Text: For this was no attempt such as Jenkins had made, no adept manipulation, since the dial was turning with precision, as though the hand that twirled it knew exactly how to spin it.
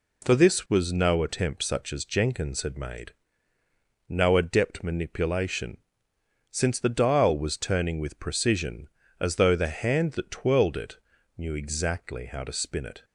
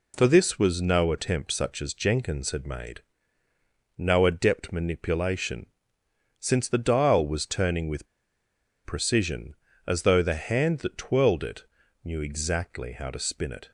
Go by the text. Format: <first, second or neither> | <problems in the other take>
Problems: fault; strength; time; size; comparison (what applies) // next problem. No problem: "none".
first | pauses between "with" and "precision"; noticeable; at 8.0 s; 0.78 s long // pauses between "it" and "knew"; at 11.6 s; 0.40 s long; also in the first